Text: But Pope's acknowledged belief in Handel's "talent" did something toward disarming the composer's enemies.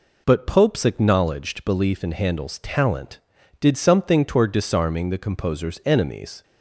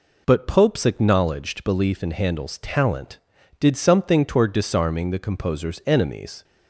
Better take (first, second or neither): neither